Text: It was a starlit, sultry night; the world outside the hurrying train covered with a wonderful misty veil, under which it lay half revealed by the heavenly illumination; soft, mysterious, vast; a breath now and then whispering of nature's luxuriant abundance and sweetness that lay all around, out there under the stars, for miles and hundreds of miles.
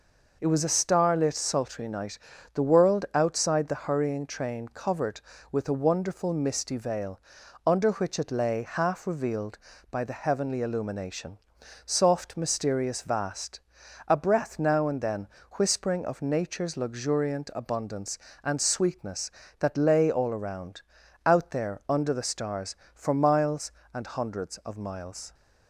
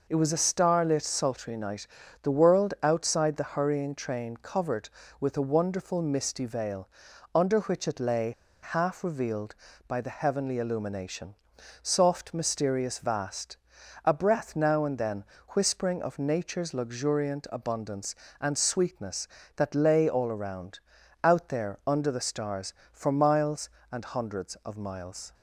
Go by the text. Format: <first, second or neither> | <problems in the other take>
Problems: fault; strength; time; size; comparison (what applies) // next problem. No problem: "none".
first | pauses between "lay" and "half"; slight; at 8.3 s; 0.31 s long // pauses between "then" and "whispering"; slight; at 15.2 s; 0.24 s long; slight in the first